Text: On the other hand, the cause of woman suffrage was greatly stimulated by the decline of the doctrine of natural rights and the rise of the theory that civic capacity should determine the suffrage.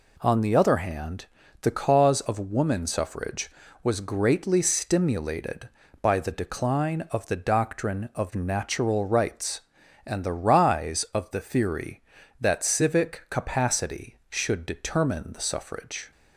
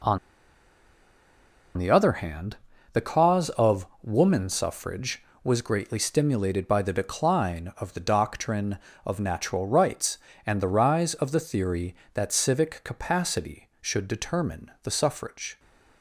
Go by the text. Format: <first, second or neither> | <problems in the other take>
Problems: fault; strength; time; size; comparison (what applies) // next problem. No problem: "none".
first | pauses between "On" and "the"; strong; at 0.1 s; 1.5 s long // pauses between "of" and "woman"; slight; at 3.8 s; 0.16 s long